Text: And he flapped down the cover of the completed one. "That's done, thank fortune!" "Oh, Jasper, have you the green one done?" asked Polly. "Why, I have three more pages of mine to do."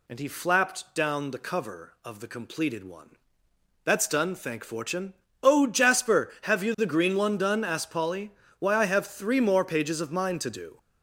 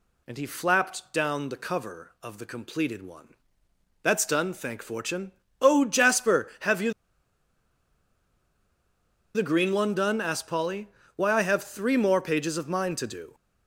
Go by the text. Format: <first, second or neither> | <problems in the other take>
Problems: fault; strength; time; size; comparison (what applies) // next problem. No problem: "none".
first | pauses between "you" and "the"; strong; at 6.9 s; 2.4 s long